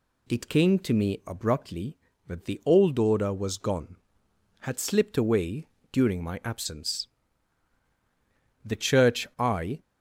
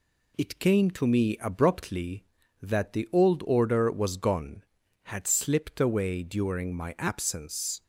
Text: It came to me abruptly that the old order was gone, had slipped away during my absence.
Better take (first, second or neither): second